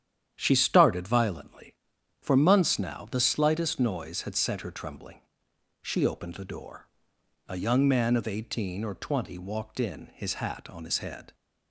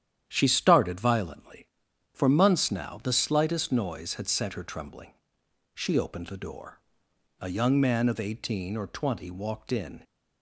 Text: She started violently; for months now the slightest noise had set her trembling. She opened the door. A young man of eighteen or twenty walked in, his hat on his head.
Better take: first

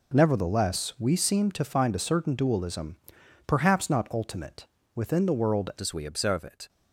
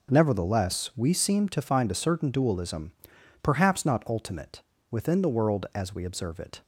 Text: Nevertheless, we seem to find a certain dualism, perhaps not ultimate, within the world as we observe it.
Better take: second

